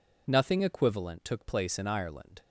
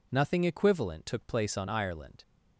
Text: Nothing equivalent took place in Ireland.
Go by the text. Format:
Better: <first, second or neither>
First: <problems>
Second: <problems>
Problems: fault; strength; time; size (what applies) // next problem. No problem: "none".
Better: first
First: none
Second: says "on" for "in"; at 1.5 s